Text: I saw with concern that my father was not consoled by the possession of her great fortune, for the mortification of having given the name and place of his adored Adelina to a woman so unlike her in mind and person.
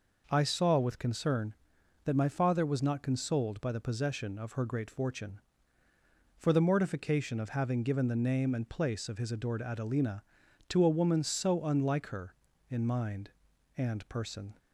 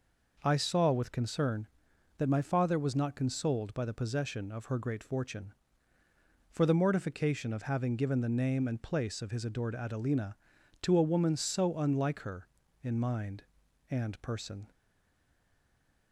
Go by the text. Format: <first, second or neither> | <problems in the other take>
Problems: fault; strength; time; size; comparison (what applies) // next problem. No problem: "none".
first | stays silent after the last word; noticeable; from 14.7 s on; 1.4 s long